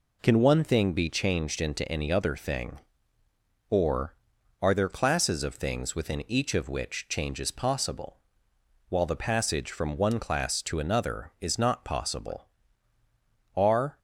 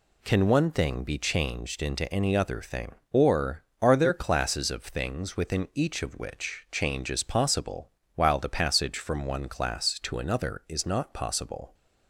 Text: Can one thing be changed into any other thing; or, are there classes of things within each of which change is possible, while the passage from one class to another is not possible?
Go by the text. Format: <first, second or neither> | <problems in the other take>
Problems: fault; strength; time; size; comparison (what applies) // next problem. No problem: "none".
second | goes on to say "Are"; slight; from 13.5 s on; 0.42 s long